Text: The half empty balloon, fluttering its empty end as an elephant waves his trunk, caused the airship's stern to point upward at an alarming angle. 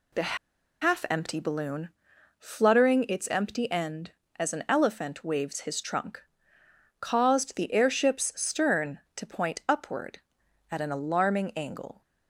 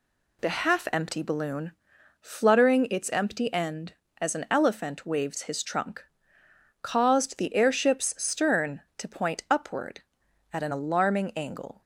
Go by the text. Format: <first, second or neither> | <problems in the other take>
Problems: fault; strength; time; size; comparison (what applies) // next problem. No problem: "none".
second | pauses between "The" and "half"; at 0.3 s; 0.44 s long